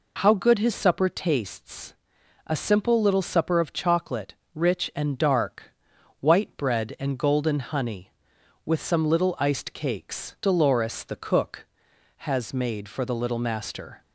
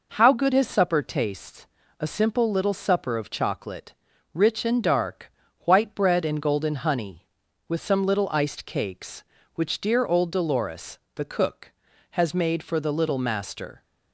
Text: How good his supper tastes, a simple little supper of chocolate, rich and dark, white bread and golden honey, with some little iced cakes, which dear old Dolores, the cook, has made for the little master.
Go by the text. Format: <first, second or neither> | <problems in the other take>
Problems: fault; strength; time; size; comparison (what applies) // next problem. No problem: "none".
second | skips "which dear old"; at 10.3 s